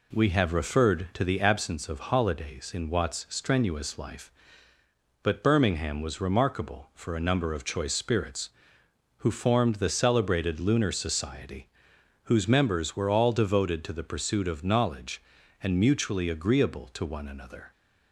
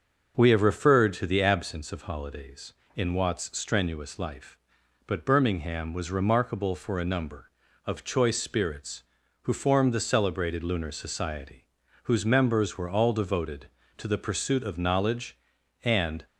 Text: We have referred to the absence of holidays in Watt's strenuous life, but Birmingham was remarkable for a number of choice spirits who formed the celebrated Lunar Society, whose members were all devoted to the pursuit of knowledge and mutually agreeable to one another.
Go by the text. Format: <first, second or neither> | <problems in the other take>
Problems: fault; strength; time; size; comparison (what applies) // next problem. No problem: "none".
first | starts louder than the rest; until 1.3 s; 6.5 dB // stops before "mutually agreeable to one another"; at 16.2 s